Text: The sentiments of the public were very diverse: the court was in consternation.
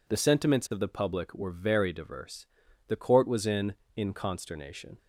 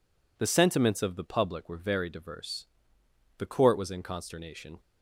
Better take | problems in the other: second | says "in" twice; at 3.9 s

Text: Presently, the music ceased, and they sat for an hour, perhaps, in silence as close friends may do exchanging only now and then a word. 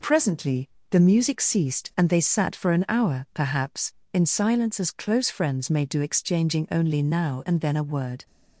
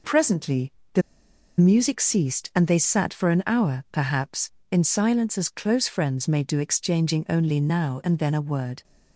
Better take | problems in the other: first | pauses between "the" and "music"; noticeable; at 1.0 s; 0.57 s long

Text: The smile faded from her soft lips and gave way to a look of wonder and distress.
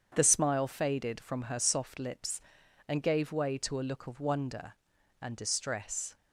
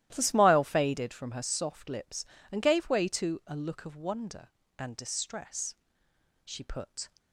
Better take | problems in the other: first | starts louder than the rest; strong; until 1.1 s; 14 dB; strong in the first // goes on to say "She put"; noticeable; from 6.4 s on; 0.68 s long

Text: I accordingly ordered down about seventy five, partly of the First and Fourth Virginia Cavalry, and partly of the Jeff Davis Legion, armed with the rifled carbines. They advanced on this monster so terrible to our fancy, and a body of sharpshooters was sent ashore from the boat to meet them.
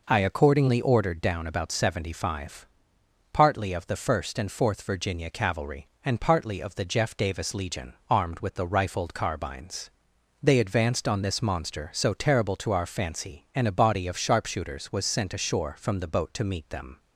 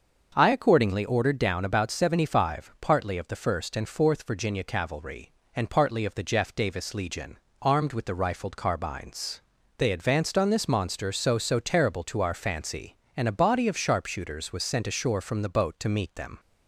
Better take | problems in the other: first | starts louder than the rest; until 1.3 s; 6.5 dB // says "so" twice; at 11.3 s

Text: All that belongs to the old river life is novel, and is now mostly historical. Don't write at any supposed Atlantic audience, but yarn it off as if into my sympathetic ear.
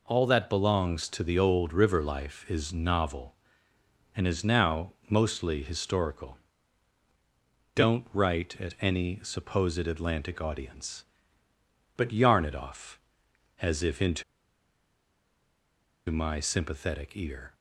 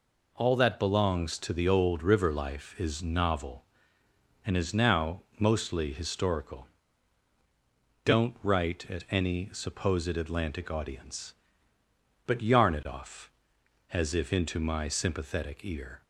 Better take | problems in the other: second | pauses between "now" and "mostly"; slight; at 4.9 s; 0.18 s long; slight in the second // pauses between "into" and "my"; strong; at 14.2 s; 1.8 s long

